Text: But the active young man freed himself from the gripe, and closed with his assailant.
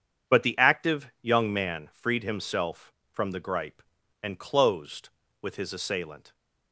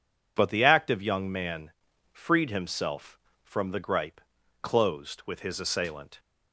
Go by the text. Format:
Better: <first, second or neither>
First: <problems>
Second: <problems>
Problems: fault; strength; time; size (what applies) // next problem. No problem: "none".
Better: first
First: none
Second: pauses between "man" and "freed"; at 1.7 s; 0.40 s long // skips "and"; at 4.4 s